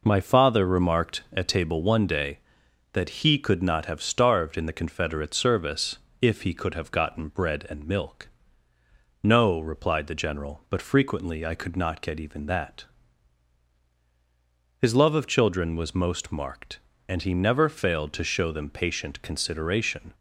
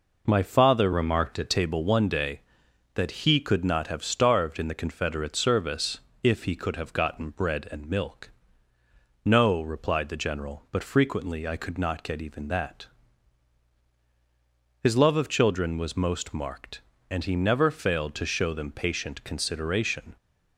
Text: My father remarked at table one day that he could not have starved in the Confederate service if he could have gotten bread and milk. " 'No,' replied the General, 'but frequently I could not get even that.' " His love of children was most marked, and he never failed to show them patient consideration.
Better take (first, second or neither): first